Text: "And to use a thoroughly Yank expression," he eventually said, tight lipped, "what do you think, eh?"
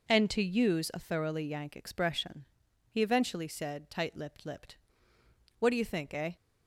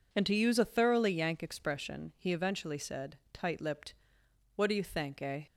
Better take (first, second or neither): second